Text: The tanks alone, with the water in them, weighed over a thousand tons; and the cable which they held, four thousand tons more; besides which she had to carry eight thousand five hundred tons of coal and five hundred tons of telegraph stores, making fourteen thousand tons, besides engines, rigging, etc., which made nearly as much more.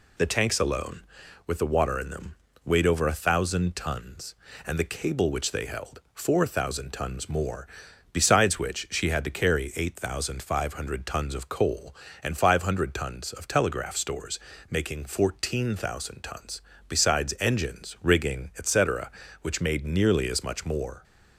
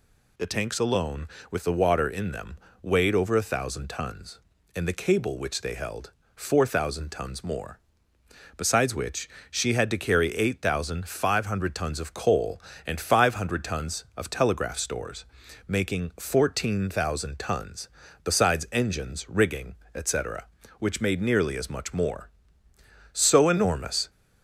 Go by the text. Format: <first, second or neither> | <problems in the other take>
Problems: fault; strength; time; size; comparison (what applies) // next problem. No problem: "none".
first | pauses between "which" and "she"; slight; at 9.2 s; 0.20 s long // goes on to say "So enormous"; noticeable; from 23.1 s on; 0.96 s long